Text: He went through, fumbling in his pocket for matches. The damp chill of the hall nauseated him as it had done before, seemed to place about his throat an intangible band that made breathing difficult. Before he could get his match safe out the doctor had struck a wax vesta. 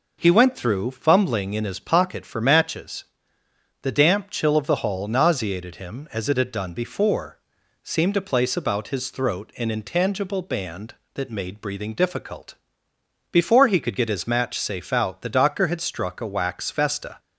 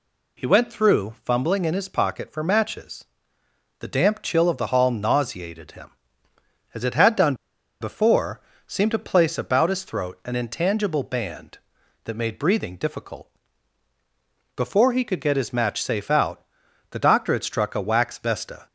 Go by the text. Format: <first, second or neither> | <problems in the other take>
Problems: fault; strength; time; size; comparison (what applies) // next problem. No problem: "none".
first | pauses between "done" and "before"; noticeable; at 7.3 s; 0.46 s long // pauses between "out" and "the"; noticeable; at 16.4 s; 0.46 s long